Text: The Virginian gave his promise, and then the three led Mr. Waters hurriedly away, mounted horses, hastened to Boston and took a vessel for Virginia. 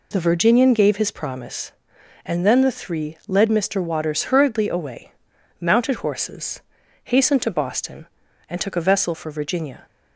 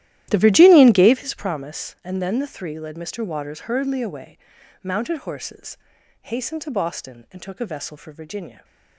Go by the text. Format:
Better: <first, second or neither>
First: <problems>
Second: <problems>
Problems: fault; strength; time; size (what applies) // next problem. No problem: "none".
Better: first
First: none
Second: starts louder than the rest; strong; until 1.3 s; 13.5 dB